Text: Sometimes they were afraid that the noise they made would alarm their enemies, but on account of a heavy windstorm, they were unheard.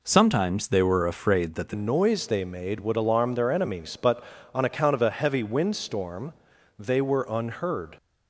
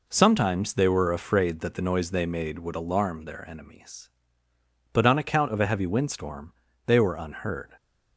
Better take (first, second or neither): second